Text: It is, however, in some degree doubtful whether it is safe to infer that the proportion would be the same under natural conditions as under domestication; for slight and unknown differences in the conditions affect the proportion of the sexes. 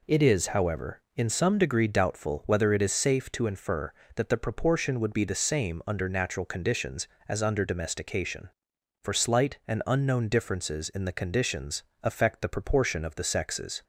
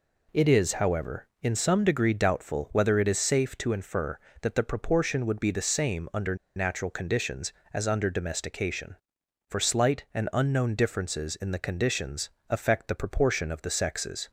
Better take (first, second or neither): first